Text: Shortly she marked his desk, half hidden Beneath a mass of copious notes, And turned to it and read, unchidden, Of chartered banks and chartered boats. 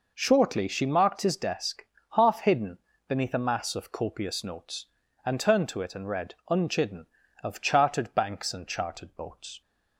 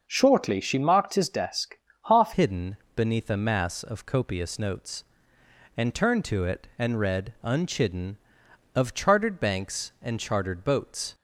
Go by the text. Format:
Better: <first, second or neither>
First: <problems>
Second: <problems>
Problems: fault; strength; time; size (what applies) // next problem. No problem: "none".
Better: first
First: pauses between "hidden" and "Beneath"; slight; at 2.7 s; 0.26 s long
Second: starts louder than the rest; until 1.0 s; 6 dB // changes voice at "hidden"; from 2.3 s on; 8.8 s long // pauses between "hidden" and "Beneath"; slight; at 2.7 s; 0.18 s long